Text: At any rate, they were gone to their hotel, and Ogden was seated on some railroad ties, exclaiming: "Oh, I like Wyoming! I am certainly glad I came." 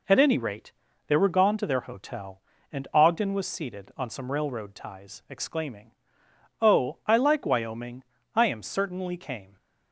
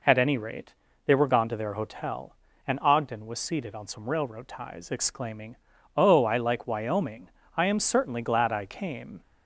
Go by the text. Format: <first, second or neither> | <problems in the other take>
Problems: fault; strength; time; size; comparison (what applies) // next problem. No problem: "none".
second | skips "glad I"; at 9.1 s